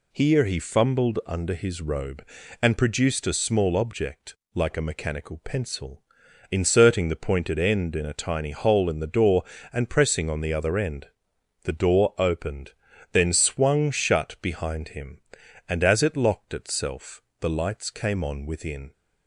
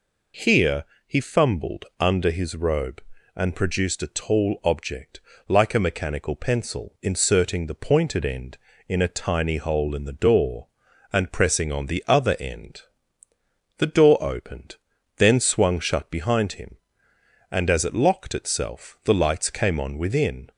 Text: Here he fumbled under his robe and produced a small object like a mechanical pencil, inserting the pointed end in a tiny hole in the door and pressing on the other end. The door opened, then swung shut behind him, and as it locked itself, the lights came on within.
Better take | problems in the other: first | pauses between "Here" and "he"; slight; at 0.8 s; 0.24 s long // says "tall" for "small"; at 4.1 s // pauses between "object" and "like"; slight; at 5.2 s; 0.26 s long; slight in the first

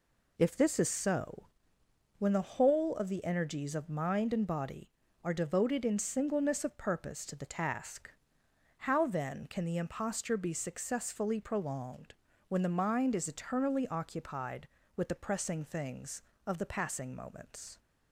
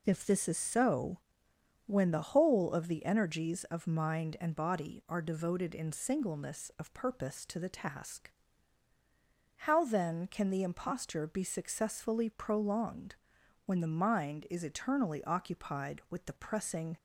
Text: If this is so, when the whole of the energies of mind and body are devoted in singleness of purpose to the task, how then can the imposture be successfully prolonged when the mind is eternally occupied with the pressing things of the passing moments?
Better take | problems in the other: first | pauses between "prolonged" and "when"; noticeable; at 13.1 s; 0.52 s long; also in the first // stops before "things of the passing moments"; at 16.9 s

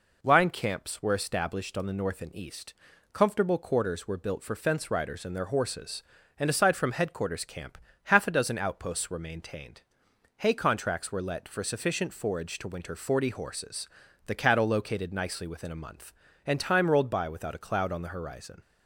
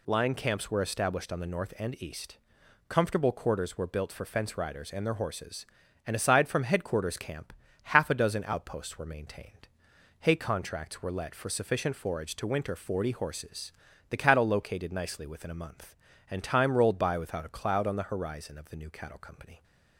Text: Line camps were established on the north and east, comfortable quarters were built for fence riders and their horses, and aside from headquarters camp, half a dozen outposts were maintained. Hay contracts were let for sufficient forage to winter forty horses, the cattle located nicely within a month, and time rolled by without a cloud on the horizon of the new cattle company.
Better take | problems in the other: second | stops before "of the new cattle company"; at 18.6 s

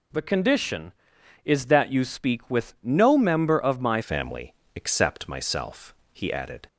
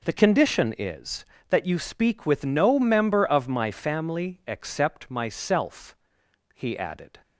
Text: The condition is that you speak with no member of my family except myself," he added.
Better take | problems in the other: second | changes voice at "family"; from 4.0 s on; 2.6 s long // pauses between "family" and "except"; slight; at 4.5 s; 0.22 s long

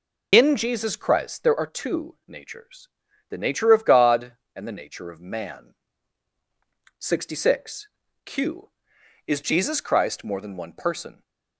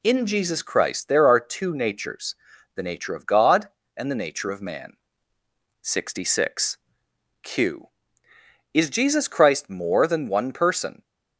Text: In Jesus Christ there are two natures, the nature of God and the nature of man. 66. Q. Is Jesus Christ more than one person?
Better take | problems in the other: second | loses the start of "In"; at 0.3 s; 65 ms

